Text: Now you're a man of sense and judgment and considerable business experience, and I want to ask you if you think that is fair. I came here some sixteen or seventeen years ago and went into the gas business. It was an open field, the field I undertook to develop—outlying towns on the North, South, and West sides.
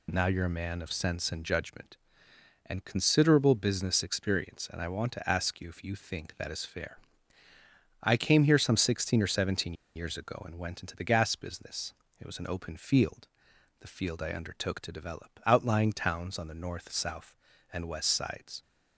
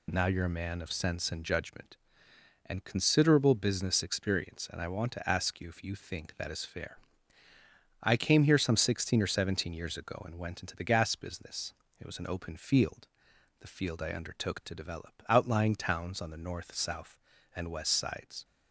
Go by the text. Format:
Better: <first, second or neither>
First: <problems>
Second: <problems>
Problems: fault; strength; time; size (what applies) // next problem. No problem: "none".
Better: second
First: pauses between "seventeen" and "years"; slight; at 9.7 s; 0.22 s long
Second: none